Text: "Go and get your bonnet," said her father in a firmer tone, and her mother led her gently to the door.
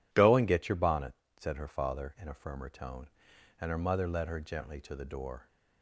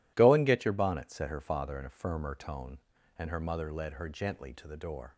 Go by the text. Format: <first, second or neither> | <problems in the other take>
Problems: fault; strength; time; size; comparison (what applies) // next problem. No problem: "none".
neither | none